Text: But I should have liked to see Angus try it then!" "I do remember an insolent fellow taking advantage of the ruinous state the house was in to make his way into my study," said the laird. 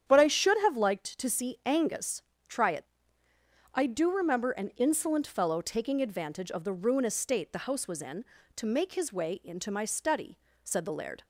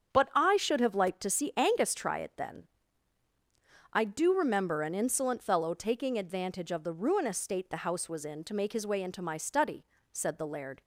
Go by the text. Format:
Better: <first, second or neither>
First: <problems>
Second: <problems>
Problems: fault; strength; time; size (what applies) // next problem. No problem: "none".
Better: second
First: starts louder than the rest; strong; until 1.1 s; 9 dB // pauses between "Angus" and "try"; slight; at 2.2 s; 0.24 s long // skips "then"; at 3.2 s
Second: starts louder than the rest; strong; until 1.1 s; 7.5 dB